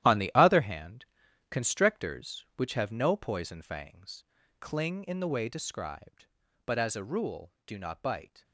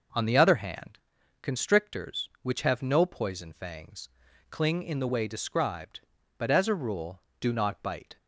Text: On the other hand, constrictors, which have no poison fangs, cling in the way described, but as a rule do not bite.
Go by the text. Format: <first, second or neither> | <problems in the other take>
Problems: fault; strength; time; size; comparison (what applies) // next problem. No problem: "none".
second | gets quieter; strong; throughout; 11 dB